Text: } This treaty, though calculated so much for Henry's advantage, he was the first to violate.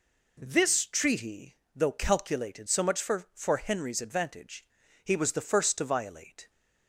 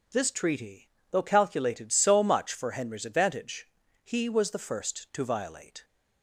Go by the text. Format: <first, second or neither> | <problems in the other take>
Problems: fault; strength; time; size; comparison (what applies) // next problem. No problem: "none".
second | says "for" twice; at 3.3 s